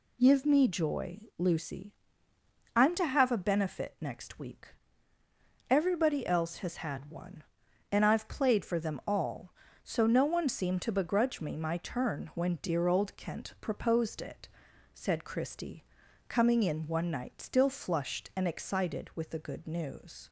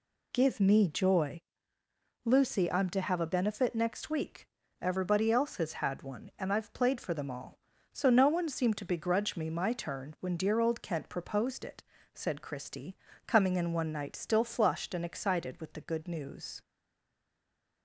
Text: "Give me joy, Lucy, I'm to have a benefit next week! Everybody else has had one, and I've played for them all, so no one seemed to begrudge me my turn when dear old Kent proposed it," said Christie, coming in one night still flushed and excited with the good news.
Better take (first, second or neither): first